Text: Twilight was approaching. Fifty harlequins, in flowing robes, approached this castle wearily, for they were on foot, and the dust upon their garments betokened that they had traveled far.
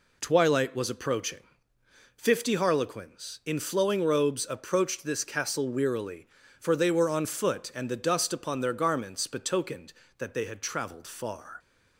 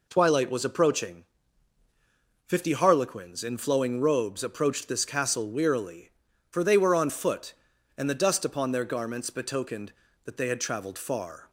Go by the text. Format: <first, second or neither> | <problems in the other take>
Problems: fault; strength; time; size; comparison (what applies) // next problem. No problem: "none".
neither | none